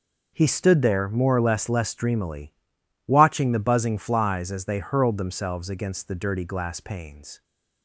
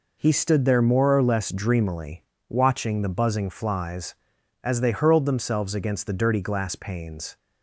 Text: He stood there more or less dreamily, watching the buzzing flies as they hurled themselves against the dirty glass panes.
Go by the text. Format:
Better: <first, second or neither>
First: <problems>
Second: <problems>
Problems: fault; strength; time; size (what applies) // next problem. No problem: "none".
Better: second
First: says "less" twice; at 1.6 s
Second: none